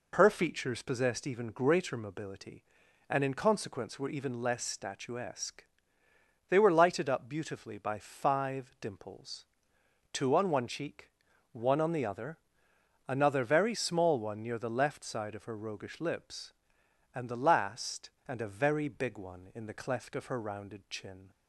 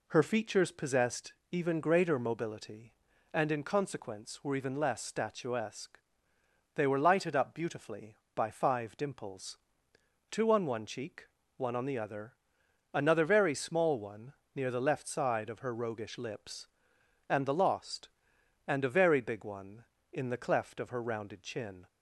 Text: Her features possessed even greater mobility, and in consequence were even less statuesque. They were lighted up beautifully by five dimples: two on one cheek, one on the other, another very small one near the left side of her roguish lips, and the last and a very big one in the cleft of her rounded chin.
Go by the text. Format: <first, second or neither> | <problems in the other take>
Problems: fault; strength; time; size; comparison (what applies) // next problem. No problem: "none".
first | pauses between "possessed" and "even"; slight; at 1.3 s; 0.18 s long // pauses between "one" and "near"; slight; at 14.3 s; 0.22 s long // says "lost" for "last"; at 17.5 s